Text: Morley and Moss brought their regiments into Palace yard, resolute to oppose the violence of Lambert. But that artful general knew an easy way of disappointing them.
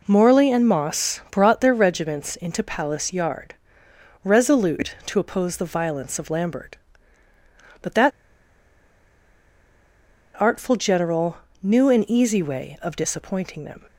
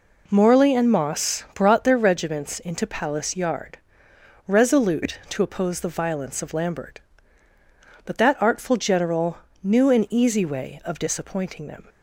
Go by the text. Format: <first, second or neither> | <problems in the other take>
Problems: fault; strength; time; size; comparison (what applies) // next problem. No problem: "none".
second | pauses between "that" and "artful"; strong; at 8.1 s; 2.2 s long // pauses between "general" and "knew"; slight; at 11.3 s; 0.24 s long; slight in the second